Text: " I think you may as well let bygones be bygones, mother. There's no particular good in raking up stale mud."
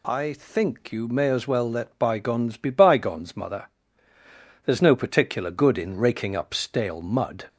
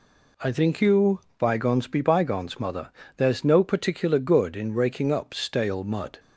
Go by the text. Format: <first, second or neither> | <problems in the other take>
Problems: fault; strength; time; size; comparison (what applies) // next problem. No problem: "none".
first | skips "may as well let"; at 1.2 s